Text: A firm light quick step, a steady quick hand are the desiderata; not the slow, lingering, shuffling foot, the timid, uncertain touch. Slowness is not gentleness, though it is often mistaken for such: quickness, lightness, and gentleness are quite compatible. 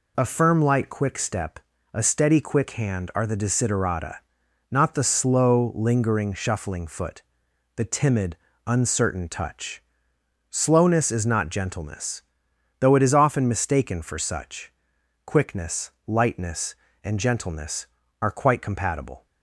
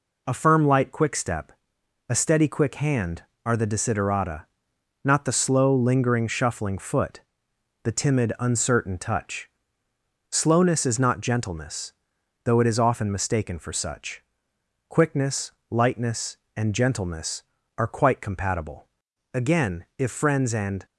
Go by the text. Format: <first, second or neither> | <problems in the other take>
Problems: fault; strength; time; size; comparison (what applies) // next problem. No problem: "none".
first | goes on to say "Again if friends and"; from 19.3 s on; 1.5 s long